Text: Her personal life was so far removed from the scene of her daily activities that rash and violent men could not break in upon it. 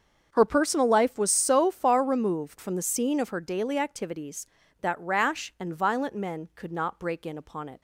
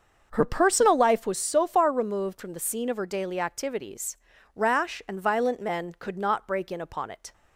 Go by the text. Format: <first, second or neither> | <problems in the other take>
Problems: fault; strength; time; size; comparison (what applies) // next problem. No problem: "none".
first | starts louder than the rest; until 1.3 s; 6.5 dB; also in the first // skips "that"; at 4.3 s